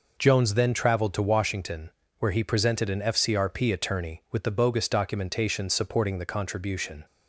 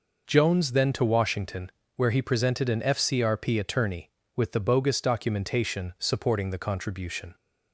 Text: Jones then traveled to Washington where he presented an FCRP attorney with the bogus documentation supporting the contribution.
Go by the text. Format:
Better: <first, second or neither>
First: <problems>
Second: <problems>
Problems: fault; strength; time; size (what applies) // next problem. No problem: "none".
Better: first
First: pauses between "Washington" and "where"; slight; at 1.9 s; 0.28 s long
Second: skips "traveled"; at 0.9 s // pauses between "Washington" and "where"; slight; at 1.7 s; 0.26 s long